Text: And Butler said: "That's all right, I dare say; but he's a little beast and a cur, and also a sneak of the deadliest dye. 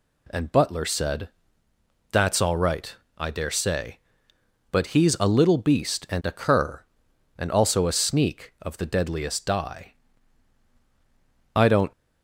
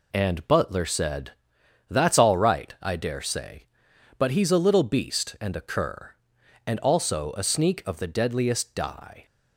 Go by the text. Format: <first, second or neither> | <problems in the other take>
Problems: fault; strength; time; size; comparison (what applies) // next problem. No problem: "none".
second | goes on to say "I don't"; slight; from 11.5 s on; 0.36 s long